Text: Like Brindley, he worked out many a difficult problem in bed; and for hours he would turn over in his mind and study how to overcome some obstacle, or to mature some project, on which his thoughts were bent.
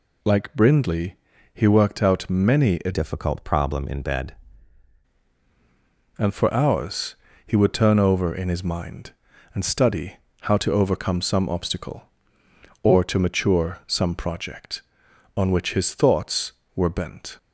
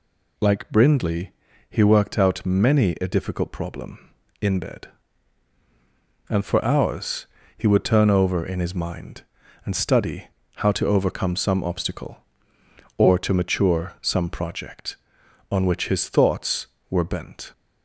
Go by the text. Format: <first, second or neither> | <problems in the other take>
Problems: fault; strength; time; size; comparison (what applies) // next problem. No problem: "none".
second | changes voice from "difficult" to "bed"; from 2.9 to 4.3 s; 1.4 s long // pauses between "hours" and "he"; slight; at 7.1 s; 0.32 s long; slight in the second // pauses between "study" and "how"; slight; at 10.1 s; 0.26 s long; slight in the second